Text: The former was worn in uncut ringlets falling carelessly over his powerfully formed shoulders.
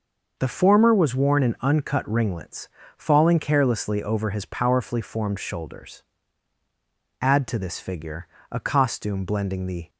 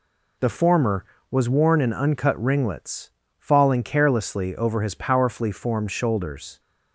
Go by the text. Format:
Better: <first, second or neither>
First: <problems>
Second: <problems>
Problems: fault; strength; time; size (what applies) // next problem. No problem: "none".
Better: second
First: pauses between "ringlets" and "falling"; slight; at 2.6 s; 0.30 s long // goes on to say "Add to this figure a costume blending the"; strong; from 7.2 s on; 2.6 s long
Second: pauses between "ringlets" and "falling"; slight; at 3.0 s; 0.30 s long